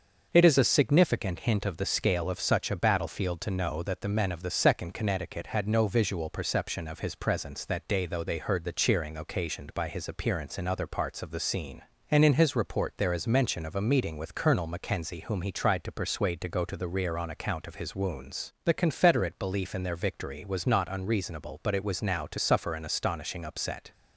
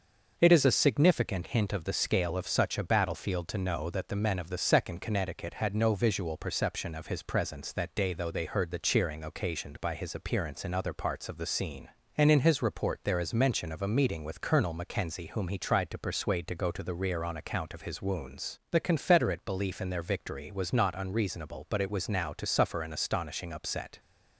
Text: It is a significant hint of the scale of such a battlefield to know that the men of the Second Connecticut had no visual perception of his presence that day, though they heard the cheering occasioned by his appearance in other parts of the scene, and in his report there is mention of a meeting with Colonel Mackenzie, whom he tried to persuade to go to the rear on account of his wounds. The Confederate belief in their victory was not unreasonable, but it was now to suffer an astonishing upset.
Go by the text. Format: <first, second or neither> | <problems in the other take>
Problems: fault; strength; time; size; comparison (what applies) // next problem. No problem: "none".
neither | starts louder than the rest; the same in both